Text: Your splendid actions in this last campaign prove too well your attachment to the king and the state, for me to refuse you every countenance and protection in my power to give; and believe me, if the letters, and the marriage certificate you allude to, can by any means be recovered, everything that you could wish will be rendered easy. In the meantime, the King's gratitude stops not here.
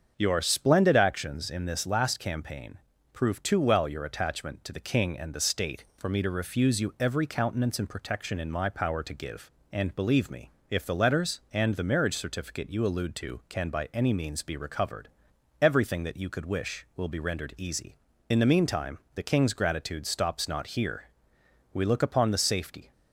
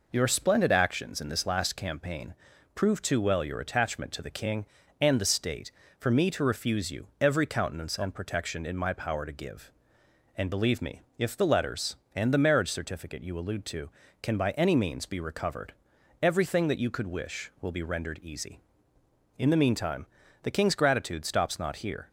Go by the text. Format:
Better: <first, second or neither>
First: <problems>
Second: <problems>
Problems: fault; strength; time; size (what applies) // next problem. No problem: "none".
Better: second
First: starts louder than the rest; strong; until 1.1 s; 7 dB // pauses between "campaign" and "prove"; slight; at 2.7 s; 0.34 s long // goes on to say "We look upon the safety"; noticeable; from 21.7 s on; 1.2 s long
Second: pauses between "campaign" and "prove"; at 2.3 s; 0.42 s long